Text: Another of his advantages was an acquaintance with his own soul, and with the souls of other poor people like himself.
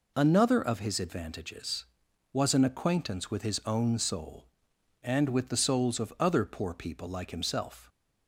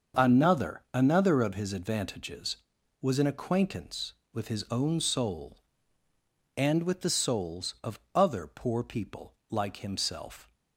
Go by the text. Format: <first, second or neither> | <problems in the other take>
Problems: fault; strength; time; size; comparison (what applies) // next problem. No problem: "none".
first | starts louder than the rest; until 1.3 s; 6.5 dB // says "Another" twice; at 0.9 s // pauses between "of" and "other"; slight; at 7.9 s; 0.16 s long // pauses between "people" and "like"; slight; at 9.3 s; 0.16 s long